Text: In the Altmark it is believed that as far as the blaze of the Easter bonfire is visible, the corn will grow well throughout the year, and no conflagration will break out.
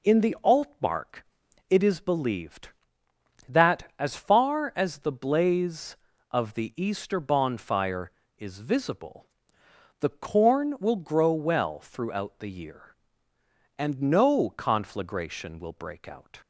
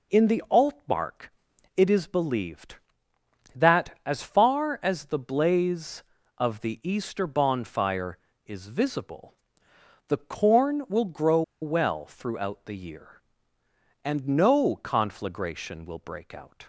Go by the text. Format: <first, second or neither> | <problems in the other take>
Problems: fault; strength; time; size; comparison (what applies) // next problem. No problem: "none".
first | pauses between "Altmark" and "it"; noticeable; at 1.2 s; 0.46 s long; noticeable in the first // pauses between "grow" and "well"; slight; at 11.4 s; 0.20 s long